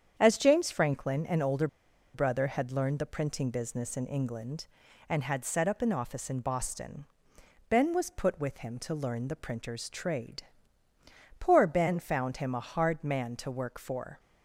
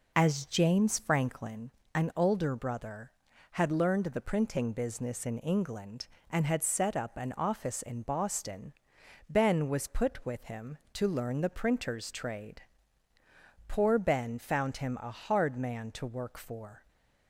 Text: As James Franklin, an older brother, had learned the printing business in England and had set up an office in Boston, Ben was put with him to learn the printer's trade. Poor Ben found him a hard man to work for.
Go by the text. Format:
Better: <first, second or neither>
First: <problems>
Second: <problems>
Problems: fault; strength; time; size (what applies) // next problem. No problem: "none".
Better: second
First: starts louder than the rest; strong; until 1.1 s; 8 dB // pauses between "older" and "brother"; noticeable; at 1.6 s; 0.47 s long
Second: none